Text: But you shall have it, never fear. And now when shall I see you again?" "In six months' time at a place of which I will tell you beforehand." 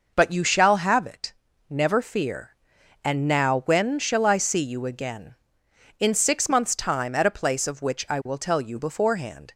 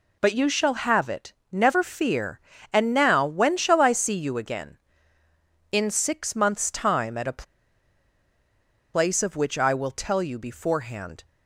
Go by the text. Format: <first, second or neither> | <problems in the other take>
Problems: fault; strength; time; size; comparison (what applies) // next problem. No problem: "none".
first | pauses between "a" and "place"; strong; at 7.4 s; 1.5 s long